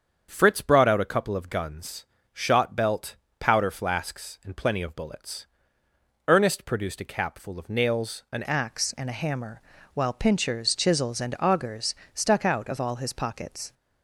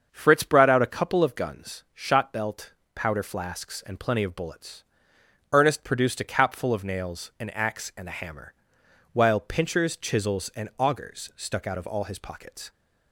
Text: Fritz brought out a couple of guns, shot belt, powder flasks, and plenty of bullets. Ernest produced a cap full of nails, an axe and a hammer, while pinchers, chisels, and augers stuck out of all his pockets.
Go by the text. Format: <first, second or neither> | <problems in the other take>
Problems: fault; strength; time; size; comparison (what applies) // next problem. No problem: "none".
second | starts louder than the rest; strong; until 1.3 s; 7 dB; also in the second // changes voice at "axe"; from 8.4 s on; 5.3 s long // pauses between "augers" and "stuck"; slight; at 11.9 s; 0.22 s long